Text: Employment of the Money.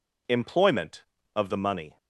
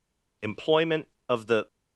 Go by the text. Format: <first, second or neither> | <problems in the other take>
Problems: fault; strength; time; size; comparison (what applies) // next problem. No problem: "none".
first | stops before "Money"; at 1.6 s